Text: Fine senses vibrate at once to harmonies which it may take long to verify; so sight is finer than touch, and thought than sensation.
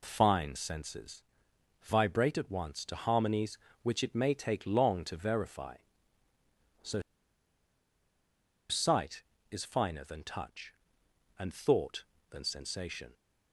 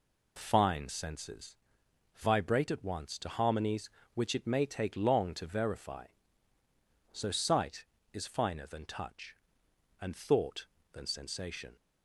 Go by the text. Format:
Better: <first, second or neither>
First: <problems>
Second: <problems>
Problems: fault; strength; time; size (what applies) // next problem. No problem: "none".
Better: second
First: pauses between "senses" and "vibrate"; noticeable; at 1.2 s; 0.58 s long // pauses between "so" and "sight"; strong; at 6.9 s; 1.6 s long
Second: pauses between "senses" and "vibrate"; noticeable; at 1.5 s; 0.58 s long